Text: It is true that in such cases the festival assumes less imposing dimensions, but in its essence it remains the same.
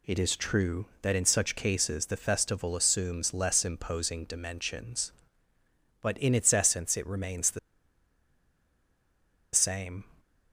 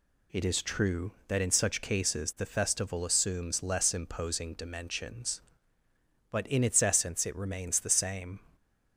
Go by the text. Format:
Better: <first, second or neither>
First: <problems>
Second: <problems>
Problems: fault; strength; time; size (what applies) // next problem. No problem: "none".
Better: second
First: pauses between "the" and "same"; strong; at 7.5 s; 1.9 s long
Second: none